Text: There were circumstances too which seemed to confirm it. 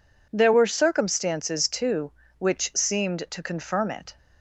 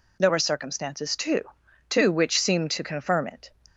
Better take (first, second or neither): first